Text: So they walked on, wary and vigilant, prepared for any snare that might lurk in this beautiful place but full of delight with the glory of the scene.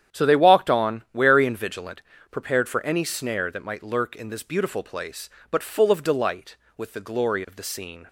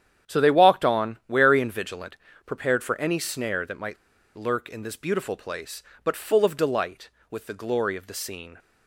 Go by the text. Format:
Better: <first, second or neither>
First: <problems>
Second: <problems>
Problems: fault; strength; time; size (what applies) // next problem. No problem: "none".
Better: first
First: starts louder than the rest; strong; until 1.2 s; 9.5 dB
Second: starts louder than the rest; strong; until 1.3 s; 9.5 dB // pauses between "might" and "lurk"; at 3.9 s; 0.40 s long